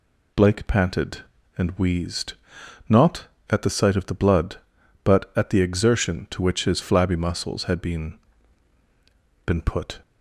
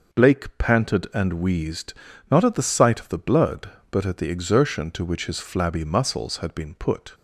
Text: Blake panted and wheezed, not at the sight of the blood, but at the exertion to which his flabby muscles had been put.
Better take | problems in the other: second | says "been" twice; at 9.4 s

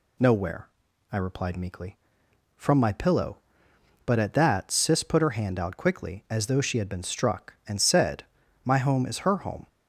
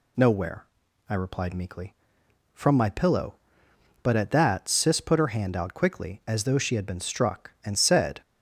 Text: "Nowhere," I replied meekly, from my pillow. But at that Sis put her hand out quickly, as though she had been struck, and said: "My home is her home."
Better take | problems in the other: first | stops before "My home is her home"; at 8.2 s

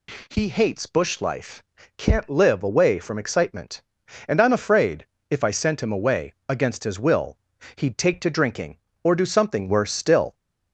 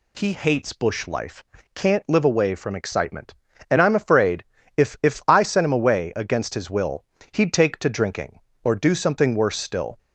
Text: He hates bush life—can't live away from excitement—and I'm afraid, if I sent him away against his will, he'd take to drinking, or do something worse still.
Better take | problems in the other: first | says "if" twice; at 5.0 s

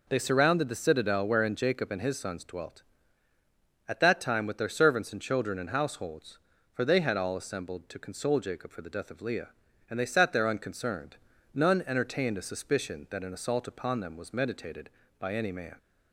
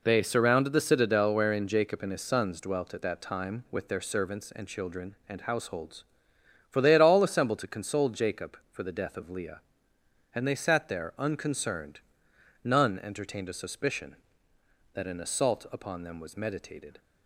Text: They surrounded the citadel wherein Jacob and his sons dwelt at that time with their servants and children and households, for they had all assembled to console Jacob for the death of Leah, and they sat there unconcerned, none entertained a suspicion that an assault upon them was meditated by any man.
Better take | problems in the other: first | stops before "by any man"; at 16.9 s

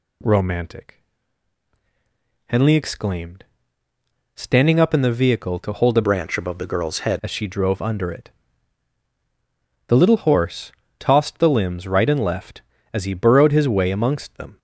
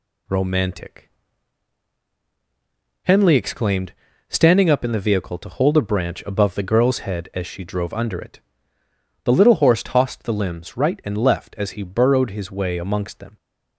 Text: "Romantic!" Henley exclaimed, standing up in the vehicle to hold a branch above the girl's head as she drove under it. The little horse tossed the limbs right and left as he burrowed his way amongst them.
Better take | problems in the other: second | changes voice from "branch" to "head"; from 6.0 to 7.1 s; 1.1 s long // pauses between "horse" and "tossed"; slight; at 10.7 s; 0.26 s long

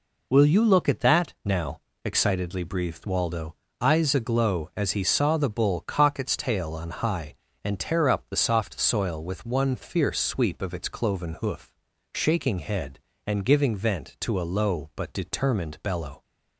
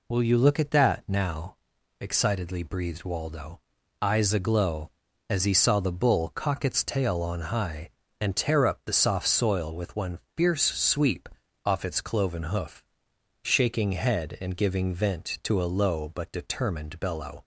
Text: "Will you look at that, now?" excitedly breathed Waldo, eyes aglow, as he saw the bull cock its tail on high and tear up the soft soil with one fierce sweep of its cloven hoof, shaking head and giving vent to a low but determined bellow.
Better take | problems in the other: first | pauses between "one" and "fierce"; slight; at 10.1 s; 0.18 s long // says "off" for "of"; at 11.6 s

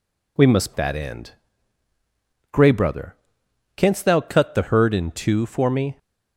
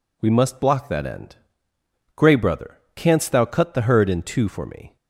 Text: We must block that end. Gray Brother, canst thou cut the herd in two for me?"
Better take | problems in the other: second | skips "block"; at 0.7 s

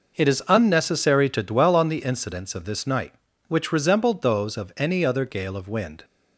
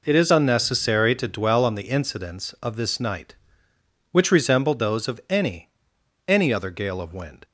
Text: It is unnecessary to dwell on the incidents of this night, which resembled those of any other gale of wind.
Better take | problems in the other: first | says "any" twice; at 6.2 s

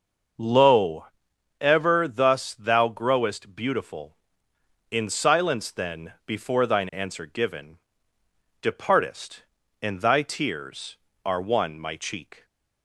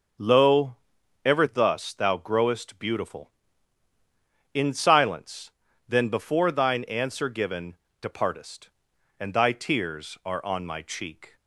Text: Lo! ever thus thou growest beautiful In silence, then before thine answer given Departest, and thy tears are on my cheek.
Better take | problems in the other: second | starts louder than the rest; until 1.9 s; 6.5 dB // pauses between "given" and "Departest"; noticeable; at 7.7 s; 0.82 s long; slight in the second // says "one" for "on"; at 11.4 s

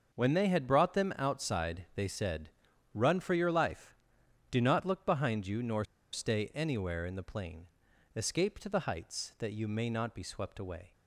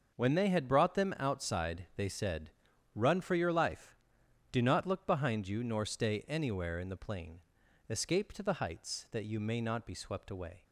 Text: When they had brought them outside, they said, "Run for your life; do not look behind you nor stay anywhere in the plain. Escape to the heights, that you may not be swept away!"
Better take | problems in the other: second | starts louder than the rest; noticeable; until 1.1 s; 6 dB; noticeable in the second // pauses between "nor" and "stay"; slight; at 5.8 s; 0.27 s long

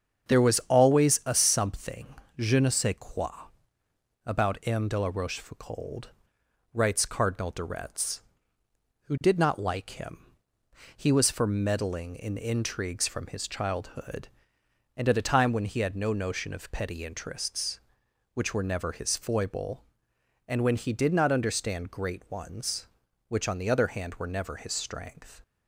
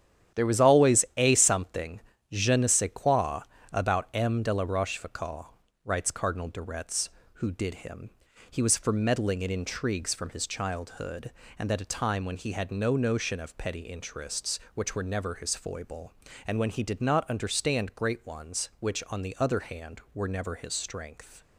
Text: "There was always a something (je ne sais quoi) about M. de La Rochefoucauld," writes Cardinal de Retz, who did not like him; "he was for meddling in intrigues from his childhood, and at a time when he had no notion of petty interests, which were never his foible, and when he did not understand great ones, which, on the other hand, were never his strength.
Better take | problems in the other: first | starts louder than the rest; strong; until 1.4 s; 10 dB; strong in the first // skips "not like"; at 7.7 s

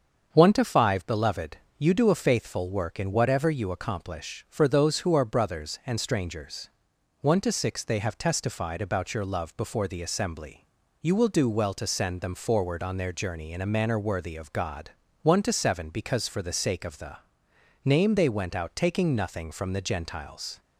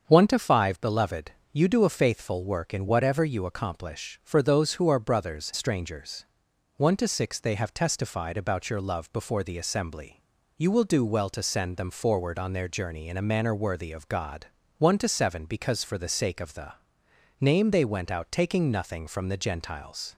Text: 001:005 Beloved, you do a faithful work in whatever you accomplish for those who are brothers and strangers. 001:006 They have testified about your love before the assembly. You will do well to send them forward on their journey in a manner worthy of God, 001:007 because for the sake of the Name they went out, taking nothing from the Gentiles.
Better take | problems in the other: first | starts louder than the rest; until 1.0 s; 7 dB; also in the first // skips "and"; at 5.5 s // pauses between "the" and "Name"; noticeable; at 16.7 s; 0.66 s long; noticeable in the first

